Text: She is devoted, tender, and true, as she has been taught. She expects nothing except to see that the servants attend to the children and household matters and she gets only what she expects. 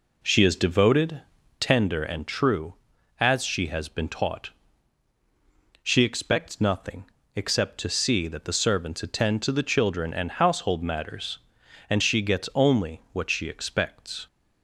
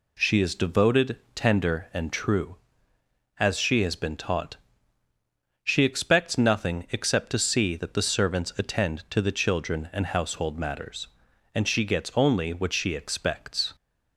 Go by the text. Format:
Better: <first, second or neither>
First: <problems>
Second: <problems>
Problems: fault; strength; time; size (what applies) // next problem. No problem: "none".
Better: second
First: starts louder than the rest; until 1.8 s; 3.5 dB // pauses between "nothing" and "except"; slight; at 7.0 s; 0.24 s long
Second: none